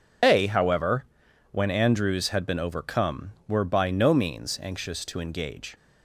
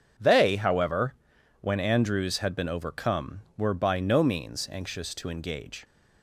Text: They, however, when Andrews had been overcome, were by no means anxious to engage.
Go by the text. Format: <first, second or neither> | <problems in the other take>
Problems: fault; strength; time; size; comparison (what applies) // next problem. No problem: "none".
second | loses the start of "They"; at 0.2 s; 135 ms